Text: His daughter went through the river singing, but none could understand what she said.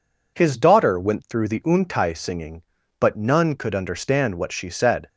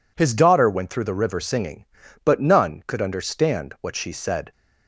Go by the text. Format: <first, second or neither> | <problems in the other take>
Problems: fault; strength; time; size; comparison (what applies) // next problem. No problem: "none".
second | says "untai" for "river"; at 1.6 s